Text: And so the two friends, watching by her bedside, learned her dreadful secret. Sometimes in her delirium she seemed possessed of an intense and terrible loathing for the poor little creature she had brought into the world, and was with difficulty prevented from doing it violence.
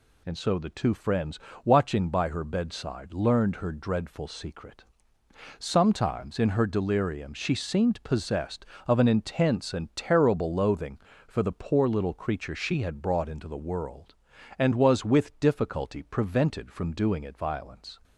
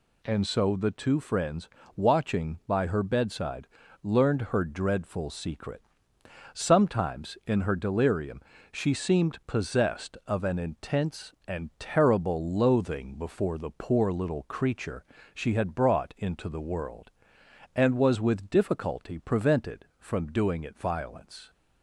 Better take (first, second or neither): first